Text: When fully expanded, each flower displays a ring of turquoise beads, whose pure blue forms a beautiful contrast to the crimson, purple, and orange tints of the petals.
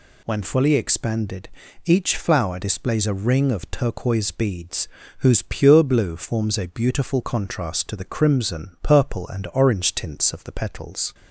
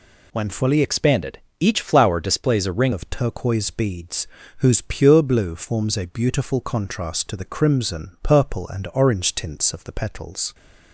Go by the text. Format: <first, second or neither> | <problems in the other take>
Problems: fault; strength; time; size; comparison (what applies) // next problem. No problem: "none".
first | changes voice from "expanded" to "ring"; from 0.8 to 2.9 s; 2.1 s long